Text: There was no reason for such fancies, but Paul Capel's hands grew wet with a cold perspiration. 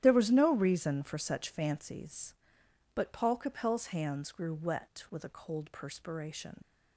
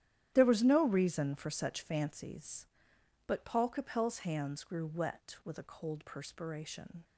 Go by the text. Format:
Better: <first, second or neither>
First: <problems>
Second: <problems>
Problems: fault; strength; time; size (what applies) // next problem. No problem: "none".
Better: second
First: starts louder than the rest; strong; until 1.0 s; 11 dB // leaves "perspiration" unfinished; at 6.6 s; 90 ms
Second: starts louder than the rest; strong; until 1.3 s; 11 dB